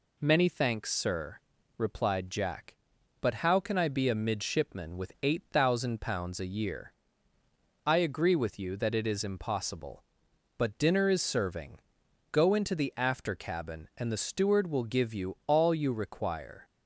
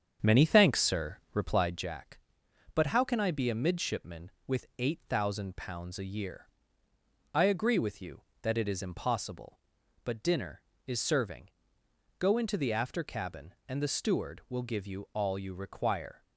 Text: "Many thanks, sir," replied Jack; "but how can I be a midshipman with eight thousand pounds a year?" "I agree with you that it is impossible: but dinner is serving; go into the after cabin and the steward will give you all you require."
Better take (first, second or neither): first